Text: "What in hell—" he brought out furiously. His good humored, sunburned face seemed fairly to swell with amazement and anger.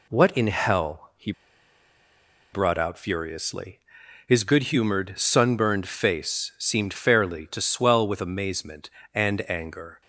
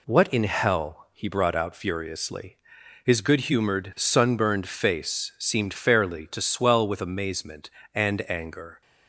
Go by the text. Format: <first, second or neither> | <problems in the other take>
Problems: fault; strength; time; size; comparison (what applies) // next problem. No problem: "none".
second | pauses between "he" and "brought"; at 1.3 s; 1.2 s long